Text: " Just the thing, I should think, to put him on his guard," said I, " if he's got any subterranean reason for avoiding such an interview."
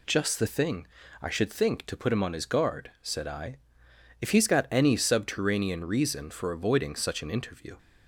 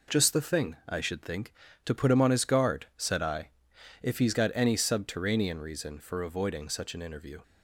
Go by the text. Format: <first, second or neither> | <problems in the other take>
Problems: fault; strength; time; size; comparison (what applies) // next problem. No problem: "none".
neither | none